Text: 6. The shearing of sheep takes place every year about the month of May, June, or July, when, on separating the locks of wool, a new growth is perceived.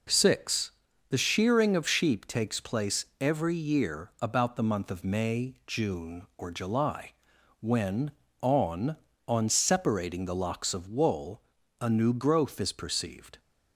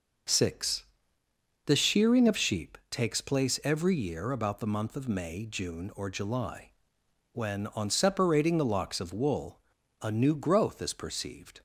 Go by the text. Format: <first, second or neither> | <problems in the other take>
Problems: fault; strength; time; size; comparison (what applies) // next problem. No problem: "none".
second | pauses between "place" and "every"; slight; at 3.0 s; 0.16 s long // says "on" twice; at 9.2 s